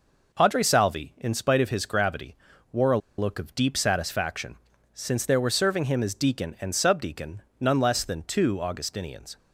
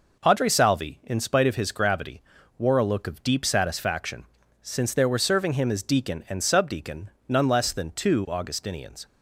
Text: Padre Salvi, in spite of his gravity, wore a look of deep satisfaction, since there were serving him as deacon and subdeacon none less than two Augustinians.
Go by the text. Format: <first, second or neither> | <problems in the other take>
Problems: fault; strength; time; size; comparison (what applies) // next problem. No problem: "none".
second | pauses between "a" and "look"; slight; at 2.9 s; 0.20 s long // pauses between "subdeacon" and "none"; slight; at 7.4 s; 0.18 s long; slight in the second